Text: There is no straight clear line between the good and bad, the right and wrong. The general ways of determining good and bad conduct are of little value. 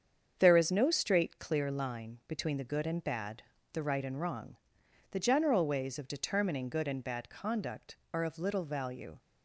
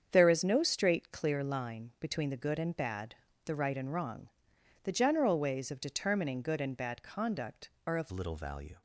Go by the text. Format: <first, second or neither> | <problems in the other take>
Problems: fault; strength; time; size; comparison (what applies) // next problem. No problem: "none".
first | starts louder than the rest; strong; until 1.1 s; 7.5 dB; strong in the first // changes voice at "little"; from 8.1 s on; 0.7 s long